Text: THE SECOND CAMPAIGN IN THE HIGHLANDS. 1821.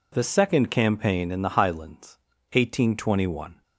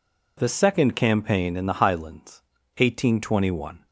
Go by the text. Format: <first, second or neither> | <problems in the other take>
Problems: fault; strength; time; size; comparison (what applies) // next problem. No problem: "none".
neither | none